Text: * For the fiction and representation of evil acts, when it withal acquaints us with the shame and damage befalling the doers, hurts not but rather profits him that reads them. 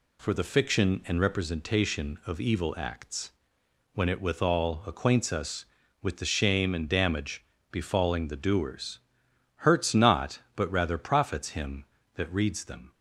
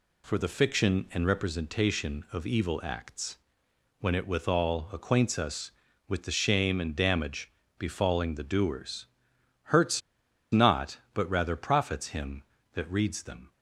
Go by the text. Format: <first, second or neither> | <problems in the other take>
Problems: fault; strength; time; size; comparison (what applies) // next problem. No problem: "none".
first | pauses between "damage" and "befalling"; slight; at 7.5 s; 0.26 s long; slight in the first // pauses between "hurts" and "not"; noticeable; at 10.0 s; 0.51 s long